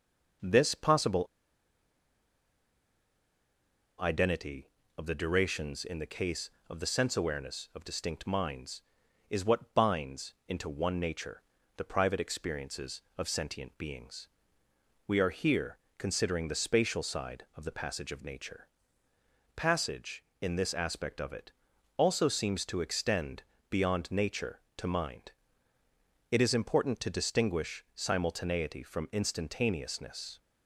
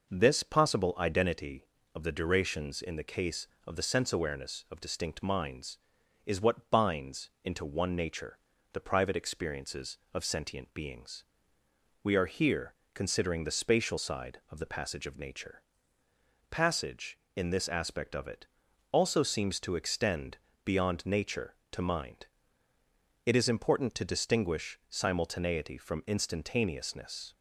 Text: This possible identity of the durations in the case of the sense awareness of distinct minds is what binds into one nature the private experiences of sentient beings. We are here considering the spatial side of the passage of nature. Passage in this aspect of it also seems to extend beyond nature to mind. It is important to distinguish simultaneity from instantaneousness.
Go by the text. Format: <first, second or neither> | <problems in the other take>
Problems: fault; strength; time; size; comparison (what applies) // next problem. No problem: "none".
second | pauses between "possible" and "identity"; strong; at 1.2 s; 2.7 s long // pauses between "nature" and "the"; slight; at 11.4 s; 0.36 s long; slight in the second // pauses between "here" and "considering"; slight; at 15.7 s; 0.18 s long; slight in the second // pauses between "it" and "also"; noticeable; at 21.5 s; 0.46 s long; noticeable in the second // pauses between "extend" and "beyond"; slight; at 23.4 s; 0.30 s long; slight in the second